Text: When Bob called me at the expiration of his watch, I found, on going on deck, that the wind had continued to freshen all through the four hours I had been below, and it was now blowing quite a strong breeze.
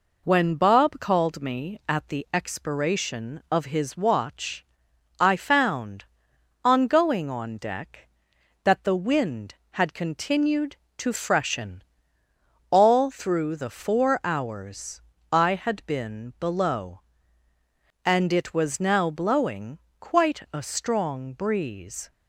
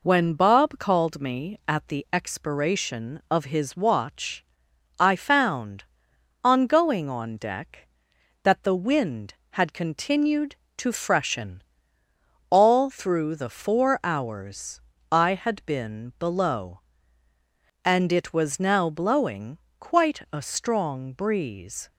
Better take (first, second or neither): neither